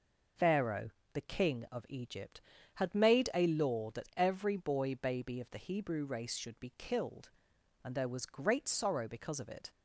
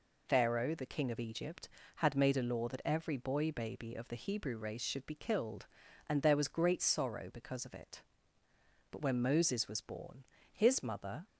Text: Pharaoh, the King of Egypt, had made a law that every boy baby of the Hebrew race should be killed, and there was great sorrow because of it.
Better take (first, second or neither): first